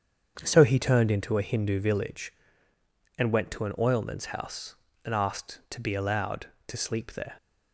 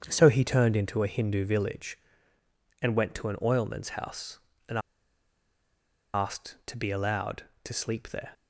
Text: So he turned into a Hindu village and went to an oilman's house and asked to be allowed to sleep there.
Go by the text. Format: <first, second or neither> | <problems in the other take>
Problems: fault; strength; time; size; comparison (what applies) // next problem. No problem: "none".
first | starts louder than the rest; strong; until 1.0 s; 7.5 dB; strong in the first // pauses between "and" and "asked"; strong; at 4.7 s; 1.3 s long